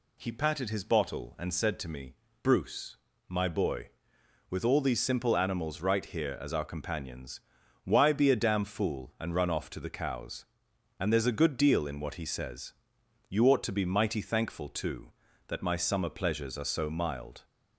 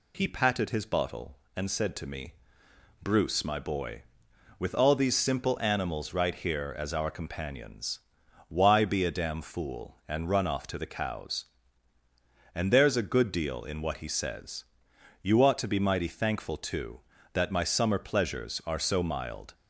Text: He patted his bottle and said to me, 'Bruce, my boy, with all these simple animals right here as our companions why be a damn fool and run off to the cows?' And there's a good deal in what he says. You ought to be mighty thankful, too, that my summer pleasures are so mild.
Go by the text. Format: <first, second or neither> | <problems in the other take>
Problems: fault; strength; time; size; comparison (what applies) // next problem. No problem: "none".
neither | pauses between "companions" and "why"; the same in both